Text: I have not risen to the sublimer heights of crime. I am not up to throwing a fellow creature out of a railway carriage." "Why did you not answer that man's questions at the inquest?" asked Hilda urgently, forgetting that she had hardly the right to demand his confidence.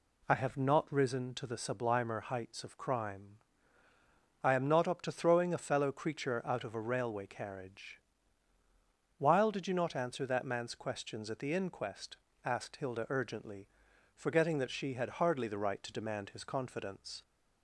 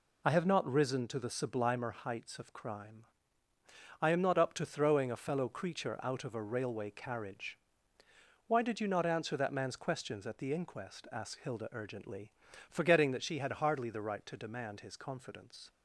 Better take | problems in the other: second | says "While" for "Why"; at 9.1 s

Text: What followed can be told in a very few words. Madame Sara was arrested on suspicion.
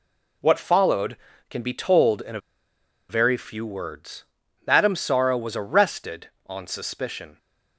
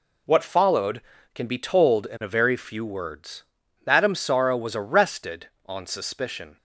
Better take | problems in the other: second | pauses between "a" and "very"; noticeable; at 2.4 s; 0.68 s long

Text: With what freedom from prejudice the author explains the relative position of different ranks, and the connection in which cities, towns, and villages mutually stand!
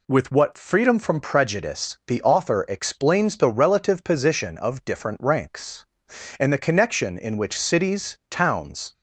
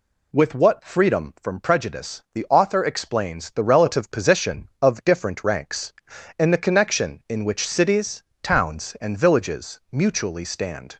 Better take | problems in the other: second | stops before "and villages mutually stand"; at 8.9 s

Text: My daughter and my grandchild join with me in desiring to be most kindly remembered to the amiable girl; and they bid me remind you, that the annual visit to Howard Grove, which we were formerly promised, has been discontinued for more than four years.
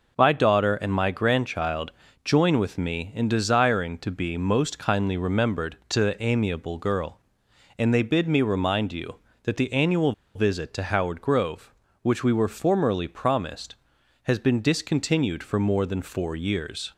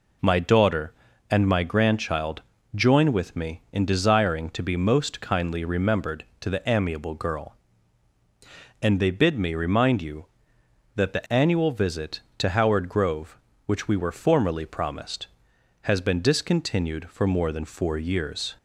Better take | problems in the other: second | pauses between "grandchild" and "join"; slight; at 1.9 s; 0.32 s long; slight in the second // pauses between "annual" and "visit"; slight; at 10.1 s; 0.22 s long

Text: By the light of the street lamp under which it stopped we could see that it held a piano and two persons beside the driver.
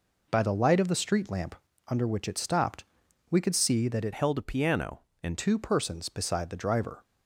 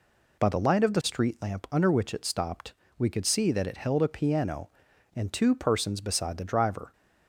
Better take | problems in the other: second | pauses between "lamp" and "under"; slight; at 1.5 s; 0.32 s long // pauses between "stopped" and "we"; noticeable; at 2.8 s; 0.46 s long; slight in the second // changes voice from "held" to "and"; from 4.1 to 5.3 s; 1.2 s long

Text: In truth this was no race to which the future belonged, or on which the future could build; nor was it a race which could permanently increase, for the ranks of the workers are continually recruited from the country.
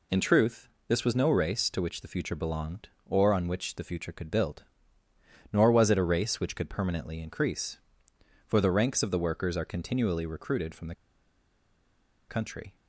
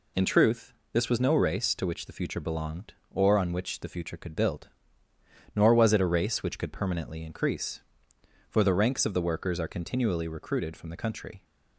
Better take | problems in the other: second | pauses between "truth" and "this"; slight; at 0.6 s; 0.20 s long; slight in the second // pauses between "the" and "country"; strong; at 10.9 s; 1.3 s long

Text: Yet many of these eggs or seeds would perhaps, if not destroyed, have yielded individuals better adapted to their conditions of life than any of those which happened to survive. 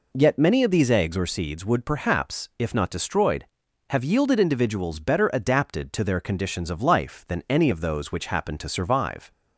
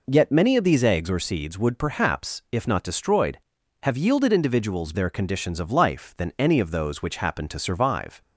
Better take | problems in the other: first | skips "better adapted to"; at 4.9 s

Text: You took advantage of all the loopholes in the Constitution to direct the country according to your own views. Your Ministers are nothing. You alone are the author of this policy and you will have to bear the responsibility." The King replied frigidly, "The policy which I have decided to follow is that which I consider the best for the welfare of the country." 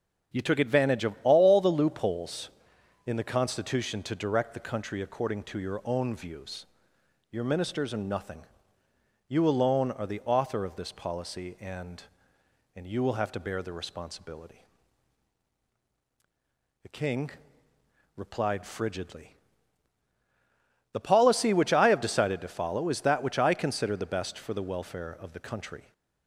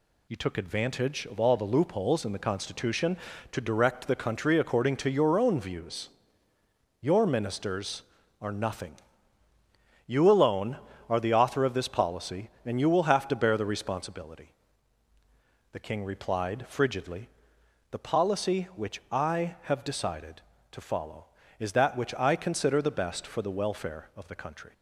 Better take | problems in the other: second | starts louder than the rest; strong; until 1.4 s; 7 dB // says "and" twice; at 12.7 s // pauses between "King" and "replied"; noticeable; at 17.3 s; 0.86 s long

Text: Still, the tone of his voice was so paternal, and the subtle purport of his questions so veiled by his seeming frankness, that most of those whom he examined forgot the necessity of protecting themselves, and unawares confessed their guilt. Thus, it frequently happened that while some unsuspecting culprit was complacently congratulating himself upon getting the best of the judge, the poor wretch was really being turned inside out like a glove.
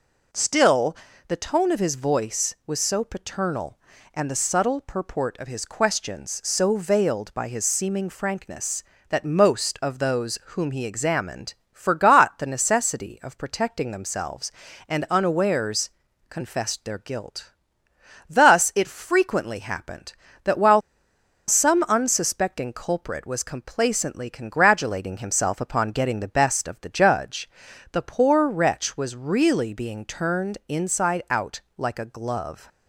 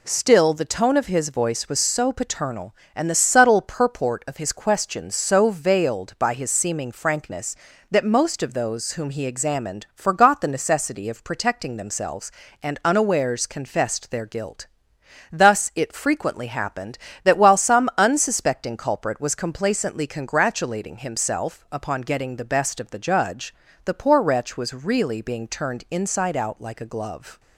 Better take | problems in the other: second | pauses between "examined" and "forgot"; slight; at 11.5 s; 0.20 s long // pauses between "unawares" and "confessed"; at 15.8 s; 0.40 s long // pauses between "while" and "some"; noticeable; at 20.7 s; 0.68 s long // pauses between "out" and "like"; slight; at 31.6 s; 0.16 s long

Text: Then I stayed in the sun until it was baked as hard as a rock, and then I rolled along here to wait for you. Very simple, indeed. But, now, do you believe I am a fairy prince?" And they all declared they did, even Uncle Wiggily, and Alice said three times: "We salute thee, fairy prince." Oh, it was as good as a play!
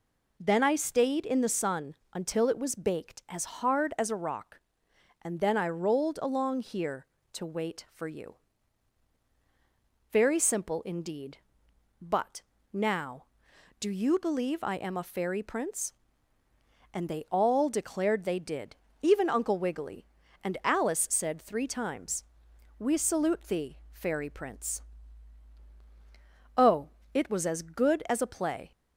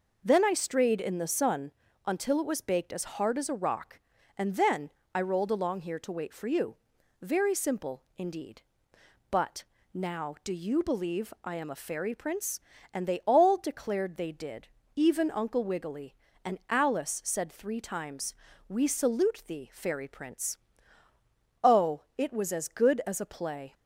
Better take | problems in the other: first | says "strayed" for "stayed"; at 0.5 s // pauses between "sun" and "until"; slight; at 1.7 s; 0.34 s long; slight in the first // pauses between "then" and "I"; slight; at 4.8 s; 0.24 s long

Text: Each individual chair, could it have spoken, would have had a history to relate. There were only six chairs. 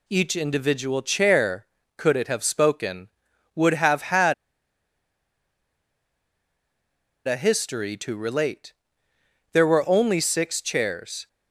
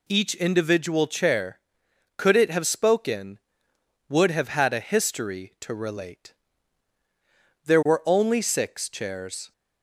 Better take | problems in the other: second | pauses between "had" and "a"; strong; at 4.3 s; 2.9 s long

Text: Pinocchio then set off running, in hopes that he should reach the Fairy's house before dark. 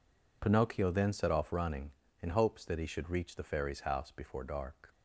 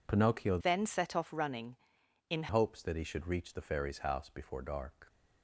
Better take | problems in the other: first | changes voice from "then" to "in"; from 0.6 to 2.4 s; 1.8 s long

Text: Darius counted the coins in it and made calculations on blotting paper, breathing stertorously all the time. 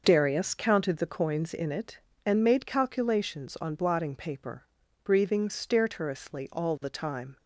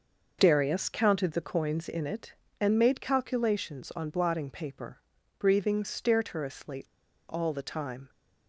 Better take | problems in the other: first | pauses between "stertorously" and "all"; noticeable; at 6.8 s; 0.48 s long

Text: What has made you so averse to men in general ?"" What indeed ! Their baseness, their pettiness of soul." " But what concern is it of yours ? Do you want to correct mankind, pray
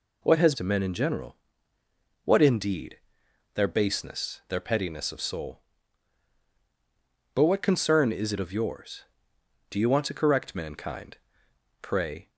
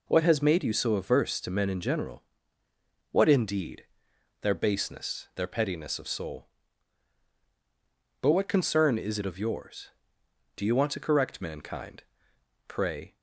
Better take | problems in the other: second | skips "made you so averse"; at 0.5 s

